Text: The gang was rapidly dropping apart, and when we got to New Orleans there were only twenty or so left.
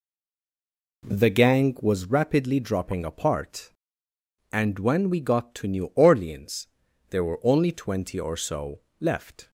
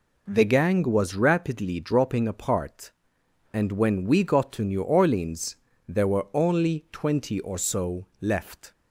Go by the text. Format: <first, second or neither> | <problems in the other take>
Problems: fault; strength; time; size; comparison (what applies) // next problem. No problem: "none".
second | stays silent before the first word; until 1.0 s; 1.0 s long // pauses between "Orleans" and "there"; at 6.6 s; 0.42 s long; slight in the second // pauses between "so" and "left"; slight; at 8.7 s; 0.20 s long; slight in the second